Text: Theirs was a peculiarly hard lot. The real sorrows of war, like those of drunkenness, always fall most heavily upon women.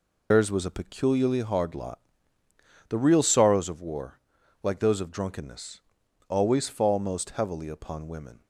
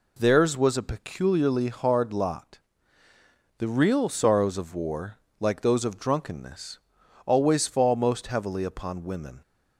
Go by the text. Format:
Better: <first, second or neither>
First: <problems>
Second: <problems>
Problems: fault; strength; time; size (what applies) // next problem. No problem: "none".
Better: second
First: loses the start of "Theirs"; at 0.3 s; 150 ms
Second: none